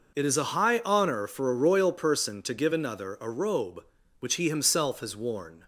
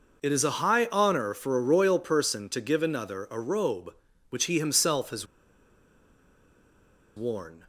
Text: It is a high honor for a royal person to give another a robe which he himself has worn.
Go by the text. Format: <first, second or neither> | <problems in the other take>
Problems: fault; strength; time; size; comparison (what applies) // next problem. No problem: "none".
first | pauses between "has" and "worn"; strong; at 5.2 s; 1.9 s long